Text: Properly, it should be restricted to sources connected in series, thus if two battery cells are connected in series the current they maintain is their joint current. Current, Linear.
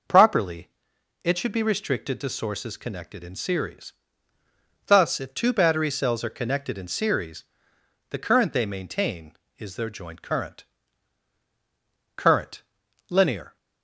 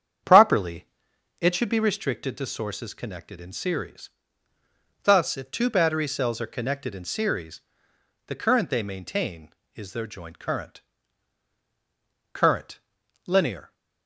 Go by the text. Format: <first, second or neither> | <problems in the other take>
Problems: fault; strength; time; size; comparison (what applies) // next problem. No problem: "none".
first | starts louder than the rest; strong; until 2.1 s; 8.5 dB // pauses between "series" and "the"; noticeable; at 7.5 s; 0.68 s long; noticeable in the first